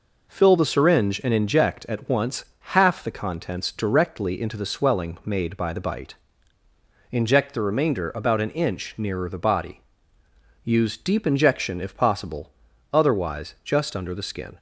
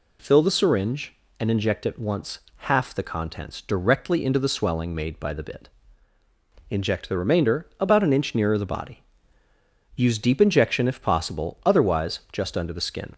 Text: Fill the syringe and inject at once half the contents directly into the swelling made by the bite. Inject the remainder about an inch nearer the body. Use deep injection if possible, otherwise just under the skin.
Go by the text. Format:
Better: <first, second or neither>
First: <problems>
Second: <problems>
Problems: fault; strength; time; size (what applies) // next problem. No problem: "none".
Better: first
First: pauses between "once" and "half"; slight; at 2.4 s; 0.28 s long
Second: pauses between "once" and "half"; slight; at 2.4 s; 0.28 s long // says "bit" for "bite"; at 5.4 s